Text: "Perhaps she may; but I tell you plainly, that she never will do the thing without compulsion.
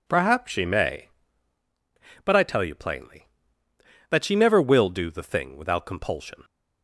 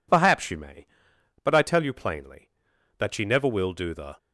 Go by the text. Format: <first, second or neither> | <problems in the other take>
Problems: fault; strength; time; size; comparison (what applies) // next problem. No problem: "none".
first | stops before "thing without compulsion"; at 4.1 s